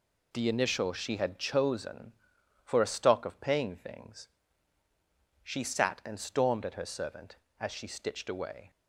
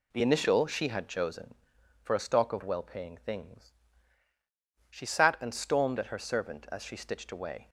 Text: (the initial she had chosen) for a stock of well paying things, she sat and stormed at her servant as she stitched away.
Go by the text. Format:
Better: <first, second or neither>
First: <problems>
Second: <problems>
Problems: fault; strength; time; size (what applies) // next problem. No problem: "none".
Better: second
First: skips "well"; at 3.3 s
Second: none